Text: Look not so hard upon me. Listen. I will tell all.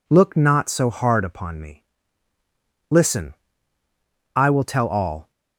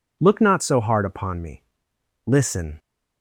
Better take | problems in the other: first | stops before "I will tell all"; at 2.7 s

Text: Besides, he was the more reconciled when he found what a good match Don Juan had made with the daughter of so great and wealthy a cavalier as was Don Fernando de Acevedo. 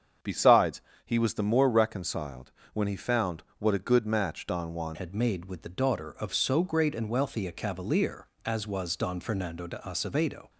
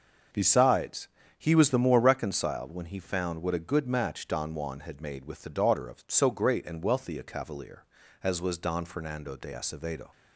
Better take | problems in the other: second | starts louder than the rest; strong; until 1.4 s; 7.5 dB; also in the second // pauses between "reconciled" and "when"; slight; at 2.5 s; 0.22 s long // pauses between "found" and "what"; slight; at 3.4 s; 0.16 s long // changes voice at "had"; from 4.9 s on; 5.5 s long

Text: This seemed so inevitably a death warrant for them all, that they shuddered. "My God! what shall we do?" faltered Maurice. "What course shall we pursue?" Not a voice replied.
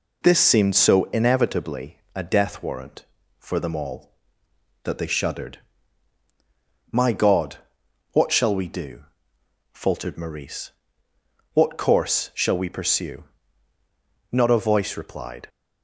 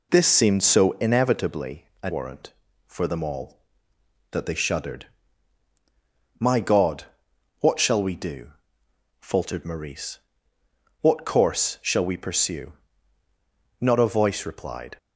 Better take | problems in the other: first | pauses between "inevitably" and "a"; slight; at 1.8 s; 0.16 s long; slight in the first // skips "death"; at 2.0 s

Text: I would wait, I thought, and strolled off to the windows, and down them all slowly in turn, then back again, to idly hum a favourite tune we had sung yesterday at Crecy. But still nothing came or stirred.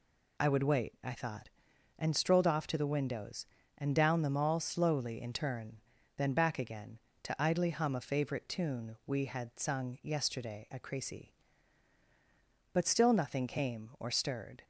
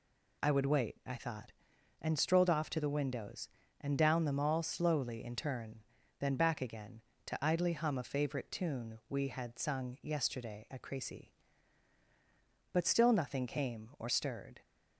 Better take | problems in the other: neither | none

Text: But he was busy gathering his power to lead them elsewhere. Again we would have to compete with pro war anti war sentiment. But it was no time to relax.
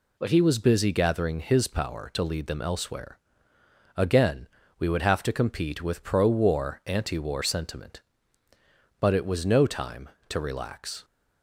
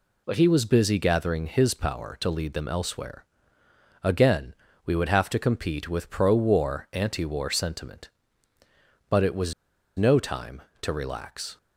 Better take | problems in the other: first | pauses between "Again" and "we"; slight; at 4.5 s; 0.30 s long; slight in the first // pauses between "was" and "no"; at 9.5 s; 0.43 s long

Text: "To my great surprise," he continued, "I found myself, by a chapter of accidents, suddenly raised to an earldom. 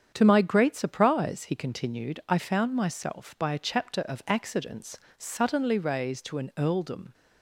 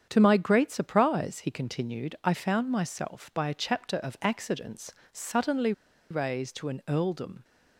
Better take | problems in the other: first | starts louder than the rest; strong; until 1.1 s; 8 dB; strong in the first // pauses between "suddenly" and "raised"; at 5.7 s; 0.38 s long

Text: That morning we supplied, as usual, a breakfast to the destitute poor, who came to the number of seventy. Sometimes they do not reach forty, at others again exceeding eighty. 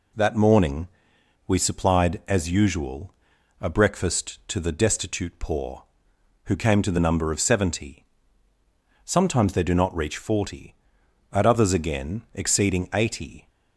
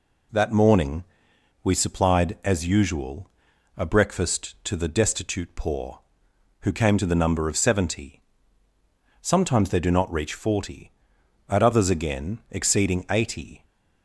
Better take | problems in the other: neither | pauses between "morning" and "we"; noticeable; the same in both

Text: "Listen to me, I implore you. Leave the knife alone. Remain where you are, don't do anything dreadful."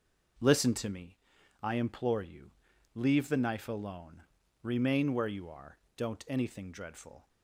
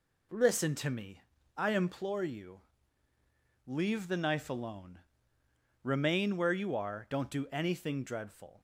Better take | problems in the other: second | skips "do"; at 6.2 s

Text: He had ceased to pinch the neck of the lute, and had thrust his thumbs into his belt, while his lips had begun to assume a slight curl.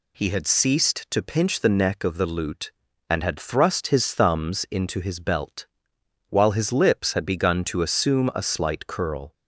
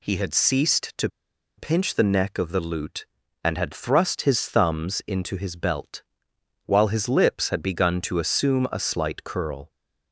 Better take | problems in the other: first | pauses between "to" and "pinch"; noticeable; at 1.0 s; 0.49 s long

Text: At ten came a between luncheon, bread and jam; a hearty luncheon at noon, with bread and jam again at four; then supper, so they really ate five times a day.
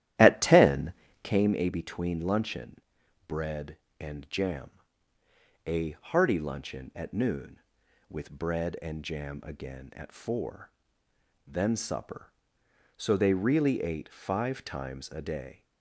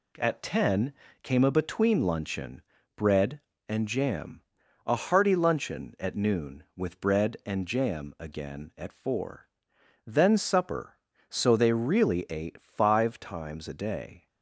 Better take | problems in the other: second | starts louder than the rest; strong; until 1.4 s; 13 dB // pauses between "ten" and "came"; slight; at 0.9 s; 0.30 s long; slight in the second

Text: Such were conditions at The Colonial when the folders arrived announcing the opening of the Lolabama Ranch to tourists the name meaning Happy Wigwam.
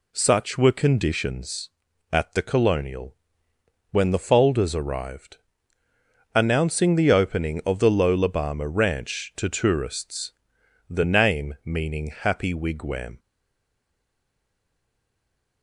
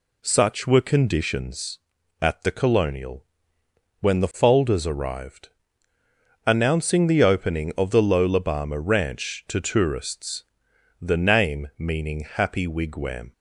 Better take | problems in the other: second | pauses between "Colonial" and "when"; noticeable; at 3.1 s; 0.76 s long; noticeable in the second // pauses between "arrived" and "announcing"; noticeable; at 5.3 s; 0.98 s long; noticeable in the second // pauses between "tourists" and "the"; noticeable; at 10.3 s; 0.56 s long; noticeable in the second // stays silent after the last word; from 13.1 s on; 2.5 s long

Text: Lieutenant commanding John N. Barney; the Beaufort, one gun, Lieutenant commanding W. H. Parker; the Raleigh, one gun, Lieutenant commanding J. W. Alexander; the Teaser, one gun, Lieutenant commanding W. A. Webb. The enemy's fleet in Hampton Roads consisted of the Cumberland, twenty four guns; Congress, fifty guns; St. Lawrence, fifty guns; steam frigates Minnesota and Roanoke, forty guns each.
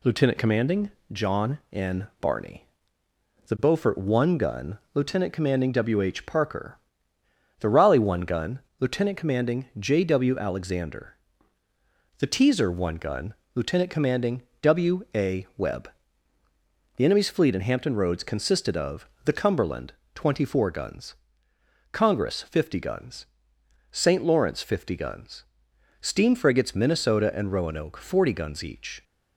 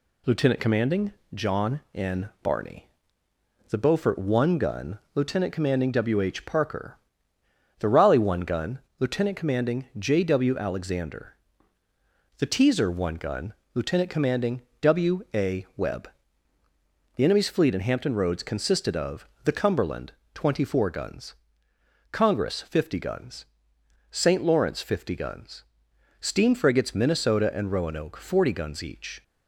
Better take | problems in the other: neither | pauses between "commanding" and "John"; slight; the same in both // pauses between "commanding" and "W"; slight; the same in both // pauses between "of" and "the"; slight; the same in both

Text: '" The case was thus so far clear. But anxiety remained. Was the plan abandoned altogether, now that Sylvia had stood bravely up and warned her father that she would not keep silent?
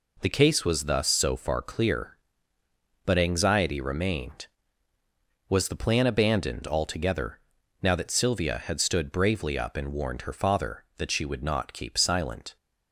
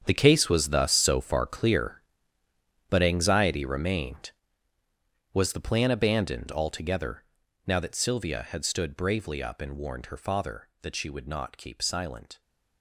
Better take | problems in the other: first | gets quieter; strong; throughout; 13.5 dB

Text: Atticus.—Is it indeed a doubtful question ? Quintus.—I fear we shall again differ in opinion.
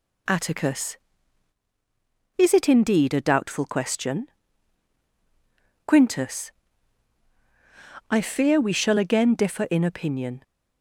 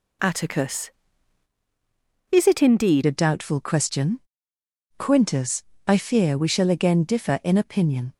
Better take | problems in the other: first | changes voice at "a"; from 3.0 s on; 5.1 s long

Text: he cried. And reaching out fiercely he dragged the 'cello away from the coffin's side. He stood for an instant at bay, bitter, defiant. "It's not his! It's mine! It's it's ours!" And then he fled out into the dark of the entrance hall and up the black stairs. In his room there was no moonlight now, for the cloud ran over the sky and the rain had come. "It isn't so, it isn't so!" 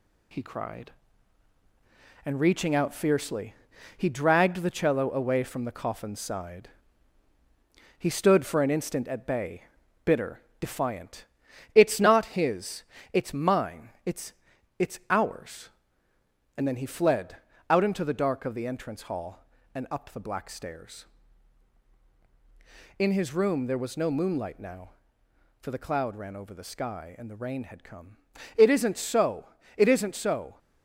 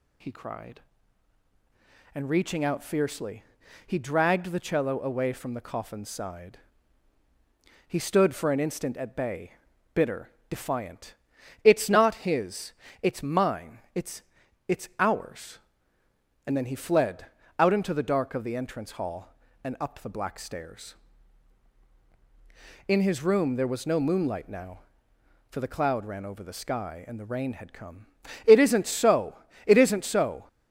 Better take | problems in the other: second | gets quieter; noticeable; throughout; 4 dB // pauses between "fiercely" and "he"; at 3.5 s; 0.44 s long; also in the second // pauses between "It's" and "it's"; noticeable; at 14.3 s; 0.46 s long; noticeable in the second // pauses between "fled" and "out"; slight; at 17.3 s; 0.32 s long; slight in the second

